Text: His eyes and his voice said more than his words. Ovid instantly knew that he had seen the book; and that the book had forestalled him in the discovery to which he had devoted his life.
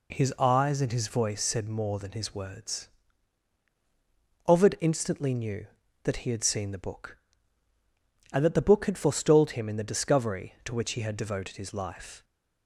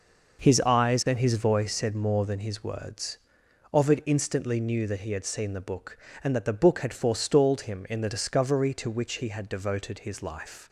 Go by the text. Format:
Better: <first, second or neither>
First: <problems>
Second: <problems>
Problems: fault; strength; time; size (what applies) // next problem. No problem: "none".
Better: first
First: none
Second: starts louder than the rest; noticeable; until 1.8 s; 5.5 dB